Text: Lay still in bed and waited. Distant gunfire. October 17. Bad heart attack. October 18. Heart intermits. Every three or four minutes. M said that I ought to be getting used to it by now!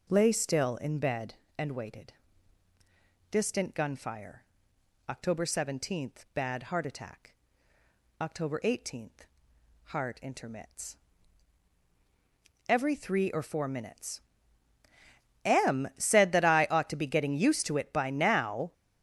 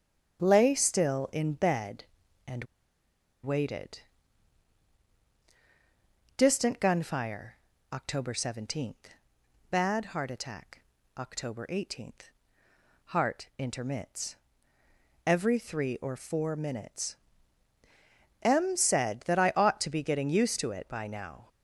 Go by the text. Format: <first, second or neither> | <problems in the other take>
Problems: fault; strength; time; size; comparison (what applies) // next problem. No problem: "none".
first | starts louder than the rest; strong; until 1.4 s; 9 dB // pauses between "and" and "waited"; noticeable; at 2.6 s; 0.78 s long